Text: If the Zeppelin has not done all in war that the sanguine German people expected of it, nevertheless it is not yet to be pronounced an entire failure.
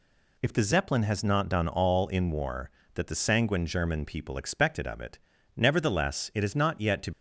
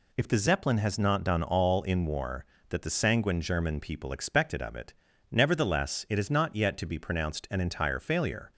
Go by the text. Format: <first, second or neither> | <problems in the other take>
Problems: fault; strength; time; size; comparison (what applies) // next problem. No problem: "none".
second | stops before "be pronounced an entire failure"; at 7.1 s